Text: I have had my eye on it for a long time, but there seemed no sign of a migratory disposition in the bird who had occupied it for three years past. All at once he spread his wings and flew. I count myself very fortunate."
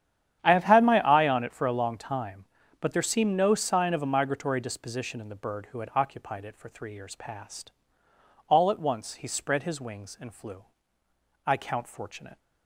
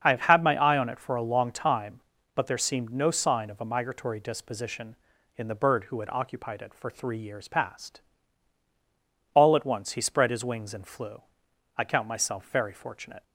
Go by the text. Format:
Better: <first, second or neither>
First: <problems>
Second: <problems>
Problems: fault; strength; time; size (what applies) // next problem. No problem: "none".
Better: second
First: starts louder than the rest; strong; until 1.4 s; 10 dB // skips "myself very"; at 11.8 s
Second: starts louder than the rest; strong; until 1.0 s; 7.5 dB